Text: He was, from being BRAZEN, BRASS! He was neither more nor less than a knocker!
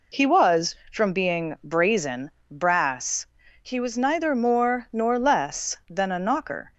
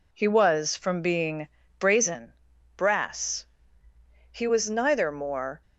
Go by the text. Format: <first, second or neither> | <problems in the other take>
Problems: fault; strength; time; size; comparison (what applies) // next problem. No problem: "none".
first | pauses between "being" and "BRAZEN"; slight; at 1.4 s; 0.32 s long // stops before "nor less than a knocker"; at 5.6 s